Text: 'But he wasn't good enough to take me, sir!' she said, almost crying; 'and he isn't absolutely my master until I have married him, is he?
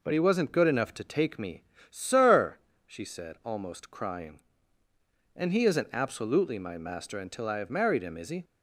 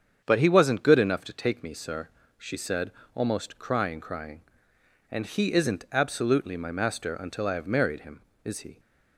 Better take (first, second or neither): first